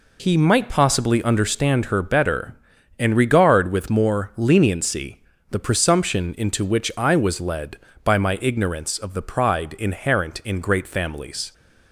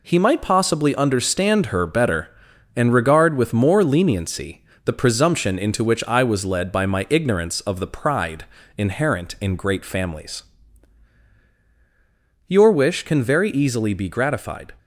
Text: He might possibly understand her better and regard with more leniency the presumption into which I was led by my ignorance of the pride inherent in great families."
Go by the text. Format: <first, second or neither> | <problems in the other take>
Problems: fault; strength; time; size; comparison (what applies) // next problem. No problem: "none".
first | pauses between "leniency" and "the"; slight; at 4.6 s; 0.22 s long; slight in the first // pauses between "pride" and "inherent"; slight; at 8.4 s; 0.32 s long // goes on to say "Your wish can very easily be gratified"; strong; from 12.4 s on; 2.2 s long